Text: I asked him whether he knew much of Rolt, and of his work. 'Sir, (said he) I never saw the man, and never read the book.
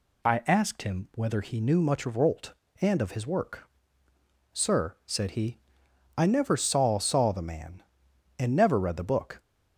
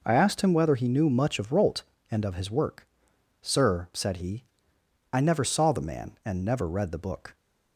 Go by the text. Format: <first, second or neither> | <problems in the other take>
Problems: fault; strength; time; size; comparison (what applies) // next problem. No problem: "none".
second | says "saw" twice; at 6.9 s